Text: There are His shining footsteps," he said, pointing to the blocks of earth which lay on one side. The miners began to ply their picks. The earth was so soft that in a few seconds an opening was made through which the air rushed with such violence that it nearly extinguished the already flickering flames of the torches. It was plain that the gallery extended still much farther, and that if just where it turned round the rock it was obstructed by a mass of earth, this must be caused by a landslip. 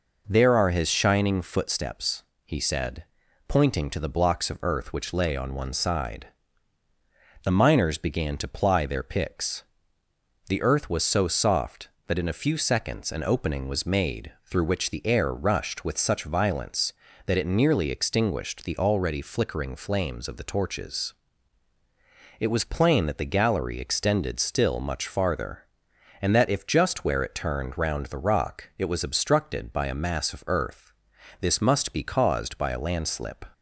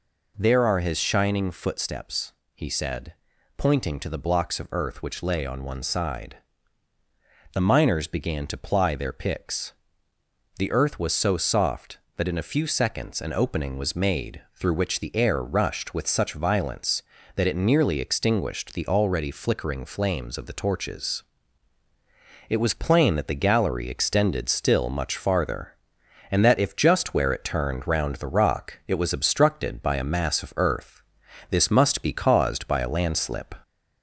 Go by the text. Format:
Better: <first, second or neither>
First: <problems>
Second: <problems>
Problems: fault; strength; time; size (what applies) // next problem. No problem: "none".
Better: first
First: pauses between "made" and "through"; slight; at 14.3 s; 0.16 s long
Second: gets louder; slight; throughout; 2 dB // pauses between "made" and "through"; slight; at 14.4 s; 0.16 s long